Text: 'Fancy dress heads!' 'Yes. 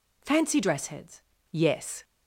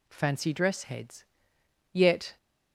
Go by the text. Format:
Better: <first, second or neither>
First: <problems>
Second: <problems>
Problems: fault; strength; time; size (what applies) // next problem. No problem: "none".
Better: first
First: none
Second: says "Yet" for "Yes"; at 1.9 s